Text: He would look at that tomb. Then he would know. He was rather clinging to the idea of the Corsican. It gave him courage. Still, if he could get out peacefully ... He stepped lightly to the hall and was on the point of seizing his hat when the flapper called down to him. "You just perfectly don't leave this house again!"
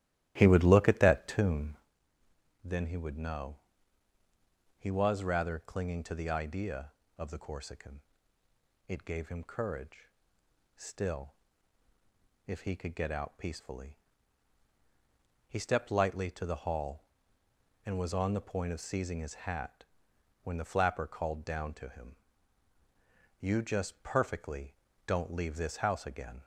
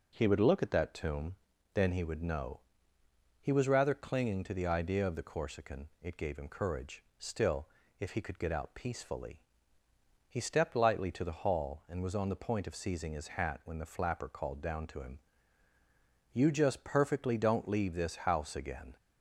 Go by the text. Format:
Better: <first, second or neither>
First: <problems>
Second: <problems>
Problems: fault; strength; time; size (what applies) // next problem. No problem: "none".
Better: second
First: starts louder than the rest; strong; until 1.9 s; 14.5 dB // pauses between "hat" and "when"; noticeable; at 19.8 s; 0.58 s long // pauses between "perfectly" and "don't"; slight; at 24.7 s; 0.32 s long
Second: none